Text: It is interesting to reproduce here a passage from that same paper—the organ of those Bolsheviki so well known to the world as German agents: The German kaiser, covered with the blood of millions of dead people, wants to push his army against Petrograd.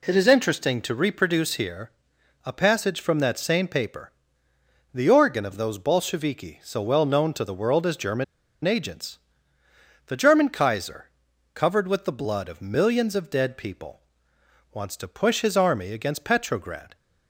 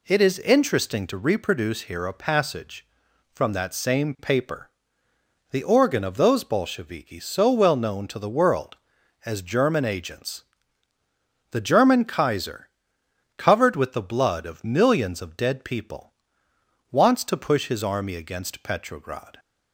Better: second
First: pauses between "here" and "a"; noticeable; at 1.8 s; 0.54 s long // pauses between "German" and "agents"; at 8.2 s; 0.40 s long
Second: none

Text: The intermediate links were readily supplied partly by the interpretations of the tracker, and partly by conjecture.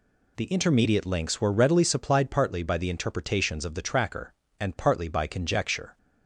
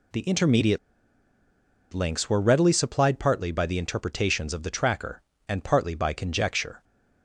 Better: first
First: none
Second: pauses between "intermediate" and "links"; at 0.7 s; 1.1 s long

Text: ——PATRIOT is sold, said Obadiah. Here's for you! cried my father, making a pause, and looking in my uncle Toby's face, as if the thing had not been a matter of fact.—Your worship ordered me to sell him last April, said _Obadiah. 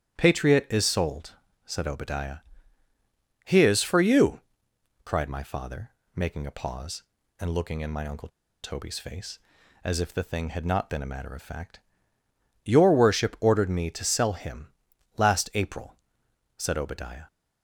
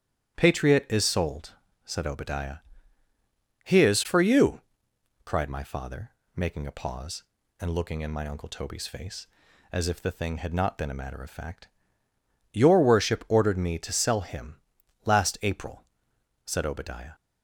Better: second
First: starts louder than the rest; strong; until 1.2 s; 10.5 dB // pauses between "uncle" and "Toby's"; slight; at 8.2 s; 0.34 s long // pauses between "him" and "last"; noticeable; at 14.7 s; 0.46 s long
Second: starts louder than the rest; strong; until 1.4 s; 10.5 dB // pauses between "him" and "last"; noticeable; at 14.5 s; 0.46 s long

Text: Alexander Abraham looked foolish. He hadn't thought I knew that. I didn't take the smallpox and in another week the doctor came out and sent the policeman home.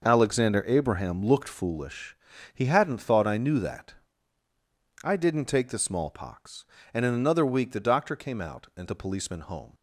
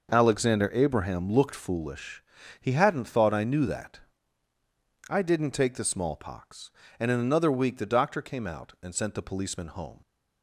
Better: second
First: skips "sent"; at 8.8 s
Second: none

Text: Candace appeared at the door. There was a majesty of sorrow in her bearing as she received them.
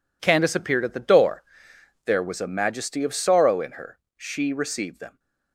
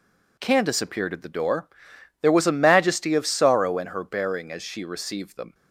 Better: second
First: skips "bearing as"; at 4.0 s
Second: none

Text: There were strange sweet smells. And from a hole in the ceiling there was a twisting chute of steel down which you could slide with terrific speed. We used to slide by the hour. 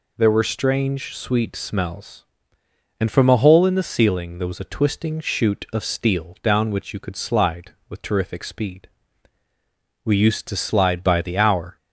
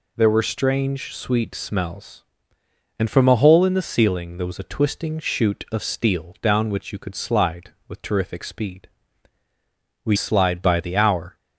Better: first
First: none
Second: skips "used to"; at 10.1 s

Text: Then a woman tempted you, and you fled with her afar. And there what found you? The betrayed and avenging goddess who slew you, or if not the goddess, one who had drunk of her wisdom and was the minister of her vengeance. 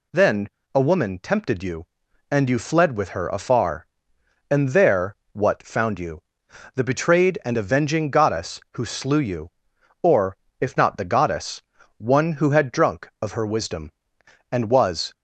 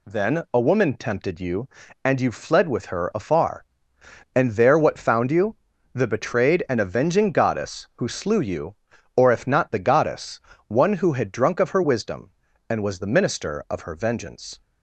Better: second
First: pauses between "Then" and "a"; slight; at 0.4 s; 0.26 s long // pauses between "there" and "what"; slight; at 5.1 s; 0.18 s long // pauses between "or" and "if"; slight; at 10.3 s; 0.24 s long // stops before "the minister of her vengeance"; at 15.1 s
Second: none

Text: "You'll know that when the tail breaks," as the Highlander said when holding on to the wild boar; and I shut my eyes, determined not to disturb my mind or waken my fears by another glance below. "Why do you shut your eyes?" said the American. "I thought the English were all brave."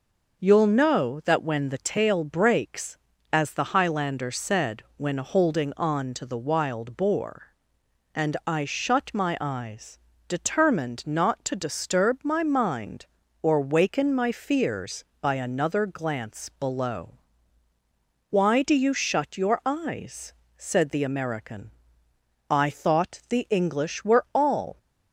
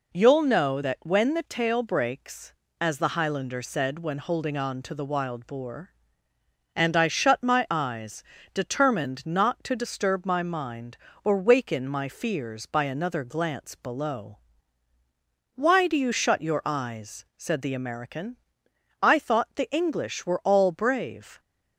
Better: second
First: stops before "brave"; at 24.7 s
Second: none

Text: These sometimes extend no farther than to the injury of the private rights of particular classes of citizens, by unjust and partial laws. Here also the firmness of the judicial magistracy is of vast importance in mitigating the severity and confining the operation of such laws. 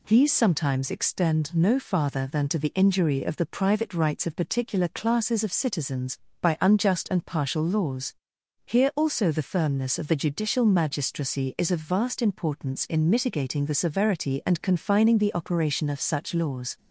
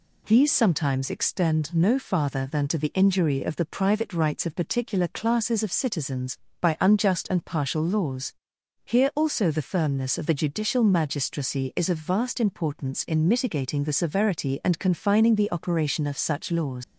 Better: first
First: none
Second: leaves "laws" unfinished; at 16.8 s; 100 ms

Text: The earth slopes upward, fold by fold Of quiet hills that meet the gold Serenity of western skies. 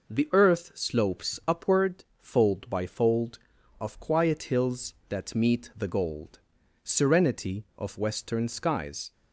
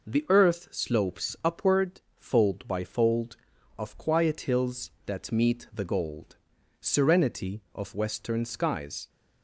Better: neither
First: pauses between "gold" and "Serenity"; at 6.3 s; 0.44 s long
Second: pauses between "gold" and "Serenity"; at 6.3 s; 0.44 s long

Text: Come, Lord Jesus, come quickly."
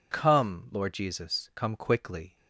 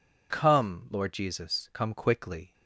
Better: neither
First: none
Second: none

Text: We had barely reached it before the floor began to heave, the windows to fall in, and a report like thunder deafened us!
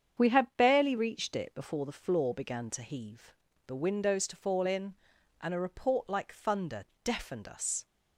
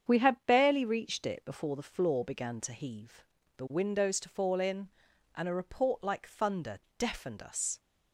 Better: neither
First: starts louder than the rest; strong; until 1.2 s; 8 dB // pauses between "thunder" and "deafened"; slight; at 6.8 s; 0.18 s long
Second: starts louder than the rest; strong; until 1.1 s; 8 dB // pauses between "thunder" and "deafened"; slight; at 6.7 s; 0.18 s long

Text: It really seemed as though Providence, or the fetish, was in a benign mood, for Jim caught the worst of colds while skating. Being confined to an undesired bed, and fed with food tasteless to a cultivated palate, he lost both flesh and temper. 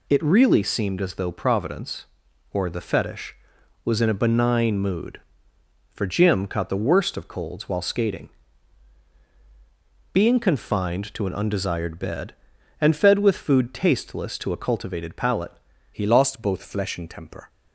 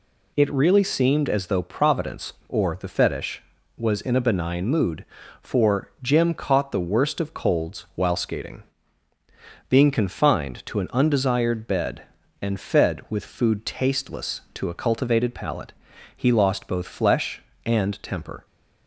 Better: second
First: changes voice at "he"; from 15.9 s on; 1.5 s long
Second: none

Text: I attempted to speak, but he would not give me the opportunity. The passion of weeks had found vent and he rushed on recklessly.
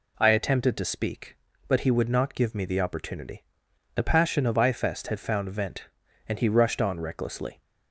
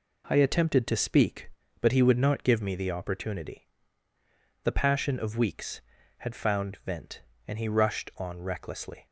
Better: second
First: says "ifest" for "weeks"; at 4.5 s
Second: none

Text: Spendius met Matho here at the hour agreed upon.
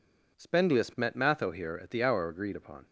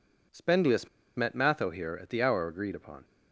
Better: first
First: none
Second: pauses between "Spendius" and "met"; slight; at 0.8 s; 0.27 s long

